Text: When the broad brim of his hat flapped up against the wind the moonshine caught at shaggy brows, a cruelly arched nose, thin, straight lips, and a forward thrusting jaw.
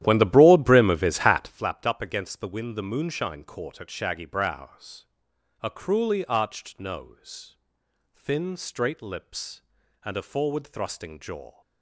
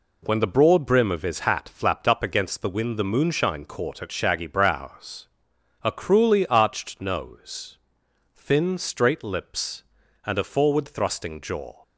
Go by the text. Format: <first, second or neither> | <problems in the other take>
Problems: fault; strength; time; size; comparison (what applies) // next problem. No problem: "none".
second | starts louder than the rest; strong; until 1.6 s; 12.5 dB